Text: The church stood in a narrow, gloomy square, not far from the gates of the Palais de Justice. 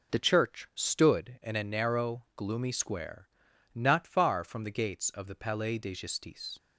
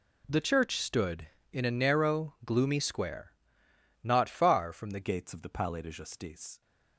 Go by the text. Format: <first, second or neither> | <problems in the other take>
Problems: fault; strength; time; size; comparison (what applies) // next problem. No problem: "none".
first | changes voice at "gates"; from 5.0 s on; 1.6 s long